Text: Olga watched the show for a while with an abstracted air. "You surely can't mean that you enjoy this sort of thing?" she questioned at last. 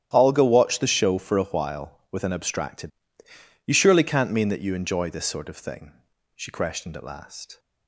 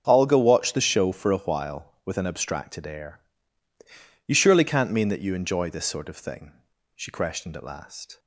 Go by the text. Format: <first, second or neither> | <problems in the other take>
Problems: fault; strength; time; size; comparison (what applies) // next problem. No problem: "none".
second | starts louder than the rest; strong; until 1.1 s; 10.5 dB; also in the second // skips "air"; at 3.2 s